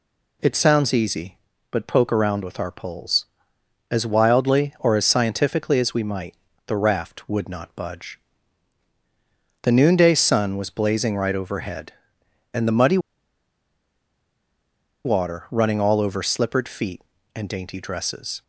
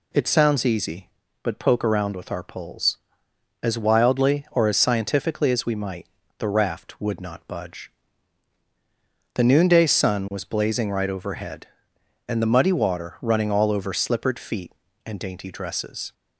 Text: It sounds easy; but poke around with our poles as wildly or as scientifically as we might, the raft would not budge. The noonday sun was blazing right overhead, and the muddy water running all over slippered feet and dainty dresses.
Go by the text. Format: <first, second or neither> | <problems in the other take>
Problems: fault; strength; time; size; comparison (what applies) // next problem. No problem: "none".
second | pauses between "muddy" and "water"; strong; at 12.9 s; 2.0 s long